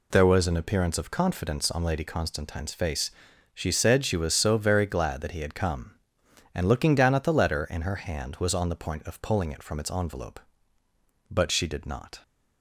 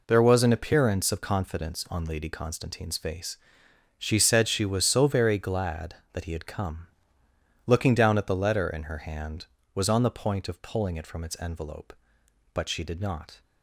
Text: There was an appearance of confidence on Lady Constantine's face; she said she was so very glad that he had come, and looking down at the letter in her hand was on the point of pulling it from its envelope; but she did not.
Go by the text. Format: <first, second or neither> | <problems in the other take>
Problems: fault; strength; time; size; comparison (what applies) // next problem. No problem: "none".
first | skips "and"; at 7.2 s